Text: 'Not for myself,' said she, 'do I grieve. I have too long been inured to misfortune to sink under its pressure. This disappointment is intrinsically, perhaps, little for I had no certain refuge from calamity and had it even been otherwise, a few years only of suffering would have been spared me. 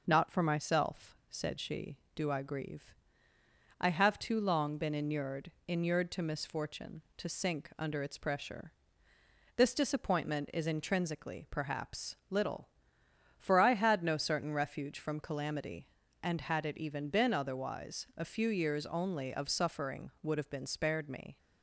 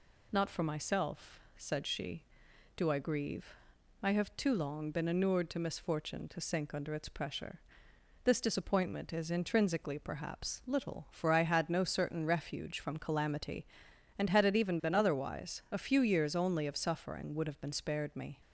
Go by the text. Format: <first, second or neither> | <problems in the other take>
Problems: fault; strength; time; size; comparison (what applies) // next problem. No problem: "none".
second | says "inured" twice; at 5.6 s